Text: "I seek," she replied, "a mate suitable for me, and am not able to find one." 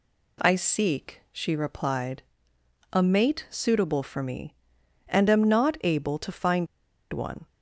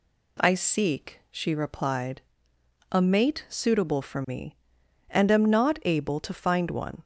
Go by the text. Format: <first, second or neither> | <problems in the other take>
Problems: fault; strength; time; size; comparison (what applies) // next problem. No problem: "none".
second | pauses between "find" and "one"; noticeable; at 6.6 s; 0.46 s long